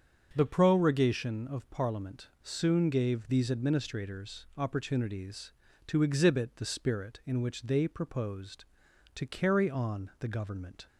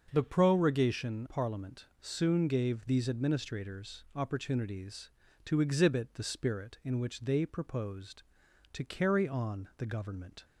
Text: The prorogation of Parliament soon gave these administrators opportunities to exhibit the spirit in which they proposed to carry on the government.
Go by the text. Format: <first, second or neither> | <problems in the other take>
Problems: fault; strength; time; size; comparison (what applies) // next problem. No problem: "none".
first | starts louder than the rest; until 1.1 s; 6.5 dB; also in the first // skips "of"; at 1.2 s // pauses between "Parliament" and "soon"; slight; at 1.8 s; 0.16 s long; slight in the first